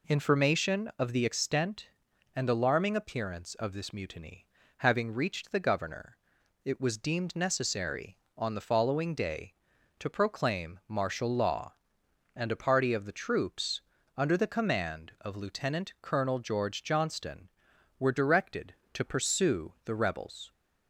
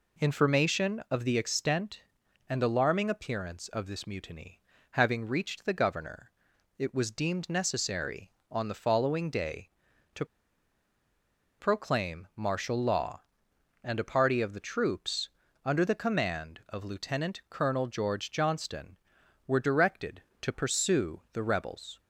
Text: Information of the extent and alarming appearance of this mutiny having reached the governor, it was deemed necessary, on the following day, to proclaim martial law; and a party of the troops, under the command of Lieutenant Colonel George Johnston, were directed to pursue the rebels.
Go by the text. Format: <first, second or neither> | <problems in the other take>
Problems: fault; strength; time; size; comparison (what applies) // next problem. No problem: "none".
first | pauses between "mutiny" and "having"; slight; at 4.5 s; 0.32 s long; slight in the first // pauses between "to" and "proclaim"; strong; at 10.2 s; 1.3 s long